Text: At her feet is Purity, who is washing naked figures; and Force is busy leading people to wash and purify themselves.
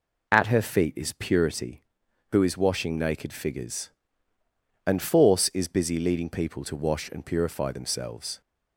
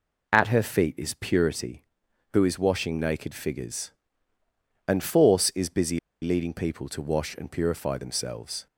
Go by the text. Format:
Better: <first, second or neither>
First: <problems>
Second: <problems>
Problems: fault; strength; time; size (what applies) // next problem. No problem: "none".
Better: first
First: none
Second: pauses between "busy" and "leading"; slight; at 5.9 s; 0.25 s long